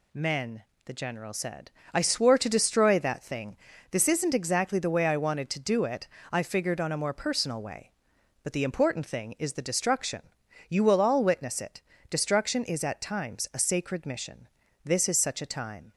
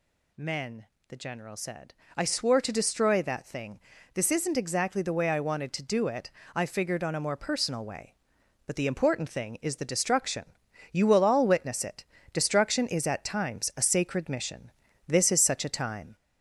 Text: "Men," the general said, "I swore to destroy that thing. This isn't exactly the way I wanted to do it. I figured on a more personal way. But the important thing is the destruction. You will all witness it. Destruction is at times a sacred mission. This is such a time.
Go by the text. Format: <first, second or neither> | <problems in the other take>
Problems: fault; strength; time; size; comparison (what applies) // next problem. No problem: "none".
first | gets louder; slight; throughout; 3 dB